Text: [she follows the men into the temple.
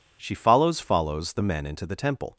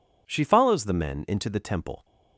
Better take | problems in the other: second | says "follows" twice; at 0.8 s

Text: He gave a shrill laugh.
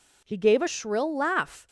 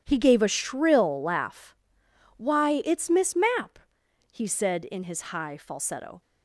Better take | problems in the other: first | starts louder than the rest; strong; until 1.0 s; 10.5 dB // goes on to say "Why it's Miss Mapp he said in his high falsetto"; strong; from 2.3 s on; 3.8 s long

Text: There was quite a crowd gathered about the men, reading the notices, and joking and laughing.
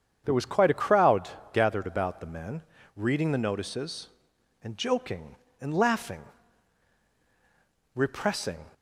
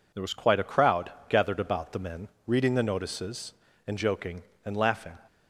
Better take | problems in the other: second | starts louder than the rest; strong; until 1.2 s; 7.5 dB // pauses between "crowd" and "gathered"; slight; at 1.2 s; 0.24 s long; slight in the second // goes on to say "Repressing"; noticeable; from 7.9 s on; 0.70 s long

